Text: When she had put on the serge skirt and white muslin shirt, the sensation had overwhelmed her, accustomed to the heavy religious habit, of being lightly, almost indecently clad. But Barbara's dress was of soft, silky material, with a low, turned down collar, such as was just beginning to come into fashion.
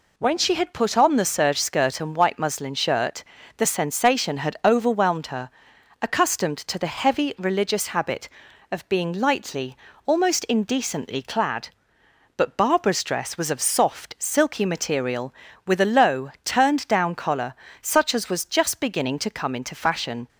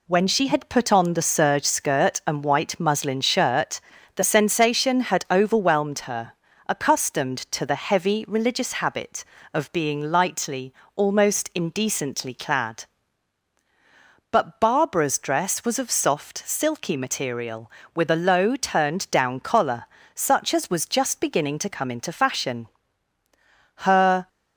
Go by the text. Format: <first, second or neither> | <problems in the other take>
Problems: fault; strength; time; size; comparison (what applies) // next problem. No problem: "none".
first | goes on to say "Her"; from 23.7 s on; 0.50 s long